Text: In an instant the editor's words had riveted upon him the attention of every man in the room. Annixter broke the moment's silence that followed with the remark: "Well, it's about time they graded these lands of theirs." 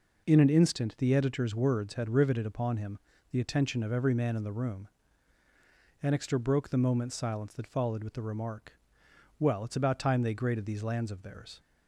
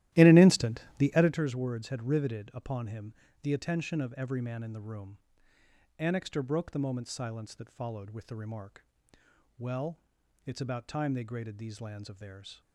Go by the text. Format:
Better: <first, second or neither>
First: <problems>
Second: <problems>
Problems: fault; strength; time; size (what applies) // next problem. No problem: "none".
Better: first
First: pauses between "him" and "the"; slight; at 2.9 s; 0.34 s long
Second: starts louder than the rest; strong; until 1.4 s; 14.5 dB // pauses between "instant" and "the"; slight; at 0.8 s; 0.16 s long // pauses between "him" and "the"; slight; at 3.1 s; 0.26 s long